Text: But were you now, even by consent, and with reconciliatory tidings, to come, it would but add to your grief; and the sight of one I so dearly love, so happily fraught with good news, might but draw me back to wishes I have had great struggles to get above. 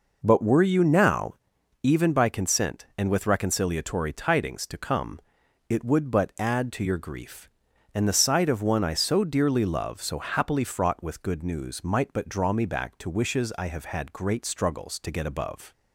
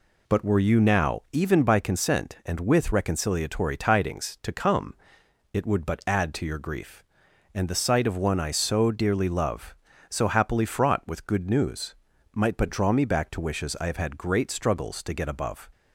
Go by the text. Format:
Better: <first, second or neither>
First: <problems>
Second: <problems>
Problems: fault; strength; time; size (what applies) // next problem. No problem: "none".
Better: neither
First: none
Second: none